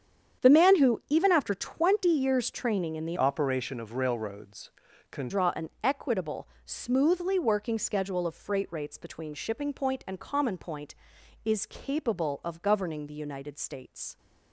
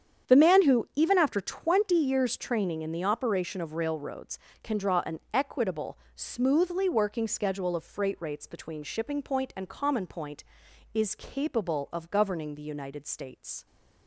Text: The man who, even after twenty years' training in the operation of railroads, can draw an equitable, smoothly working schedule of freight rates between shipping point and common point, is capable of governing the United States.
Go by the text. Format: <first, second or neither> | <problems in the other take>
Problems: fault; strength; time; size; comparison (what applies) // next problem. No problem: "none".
second | starts louder than the rest; strong; until 1.4 s; 8.5 dB; strong in the second // changes voice from "operation" to "can"; from 3.1 to 5.2 s; 2.1 s long // pauses between "an" and "equitable"; slight; at 5.6 s; 0.16 s long; slight in the second